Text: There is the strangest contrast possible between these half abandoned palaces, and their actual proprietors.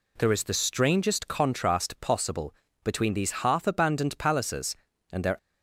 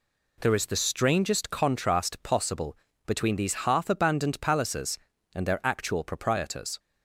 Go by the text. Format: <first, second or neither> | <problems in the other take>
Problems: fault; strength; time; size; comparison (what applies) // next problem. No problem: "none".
second | pauses between "possible" and "between"; slight; at 2.5 s; 0.30 s long; slight in the second // stops before "actual proprietors"; at 5.3 s